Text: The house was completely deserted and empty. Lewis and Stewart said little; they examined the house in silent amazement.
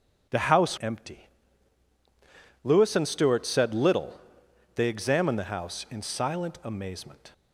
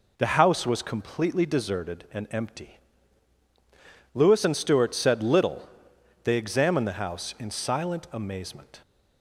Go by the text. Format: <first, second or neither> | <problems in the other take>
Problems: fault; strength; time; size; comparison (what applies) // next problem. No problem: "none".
second | skips "was completely deserted and"; at 0.7 s